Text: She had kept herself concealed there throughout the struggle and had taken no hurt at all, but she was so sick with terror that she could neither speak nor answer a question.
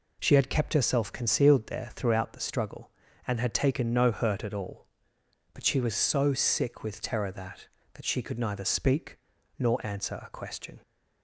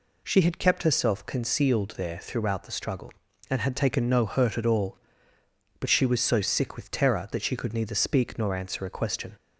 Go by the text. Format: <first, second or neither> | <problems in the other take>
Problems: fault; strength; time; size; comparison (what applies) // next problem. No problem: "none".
second | says "that" twice; at 7.9 s // pauses between "speak" and "nor"; at 9.1 s; 0.40 s long